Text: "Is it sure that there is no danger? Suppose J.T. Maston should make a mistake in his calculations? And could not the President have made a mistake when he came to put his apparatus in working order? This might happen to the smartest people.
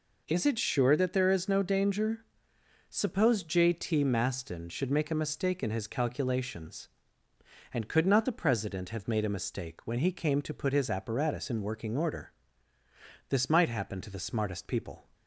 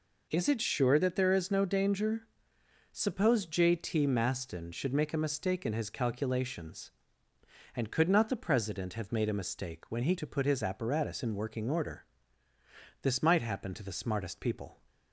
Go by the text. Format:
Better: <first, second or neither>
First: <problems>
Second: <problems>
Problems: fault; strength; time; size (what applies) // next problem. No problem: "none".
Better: first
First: none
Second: skips "came"; at 10.1 s